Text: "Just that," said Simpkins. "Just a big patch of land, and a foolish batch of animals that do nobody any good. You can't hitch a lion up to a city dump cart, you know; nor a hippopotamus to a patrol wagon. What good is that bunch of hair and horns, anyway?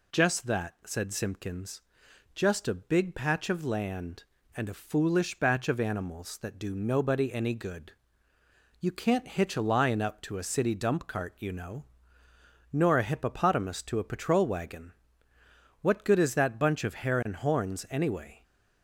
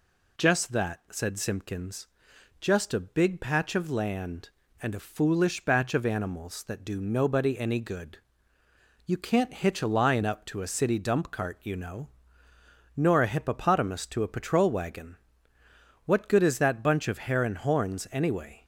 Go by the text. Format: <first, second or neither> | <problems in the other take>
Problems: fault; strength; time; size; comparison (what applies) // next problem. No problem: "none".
neither | none